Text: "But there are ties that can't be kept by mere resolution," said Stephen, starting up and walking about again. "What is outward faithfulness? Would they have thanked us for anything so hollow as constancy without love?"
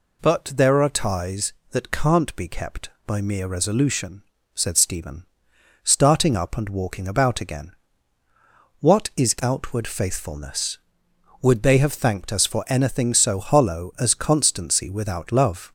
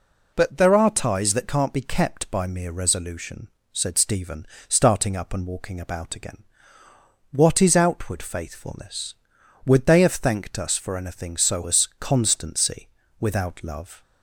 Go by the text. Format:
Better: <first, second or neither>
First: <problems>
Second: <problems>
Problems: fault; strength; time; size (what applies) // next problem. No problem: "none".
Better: first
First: none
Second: skips "hollow"; at 11.6 s // pauses between "constancy" and "without"; slight; at 12.8 s; 0.32 s long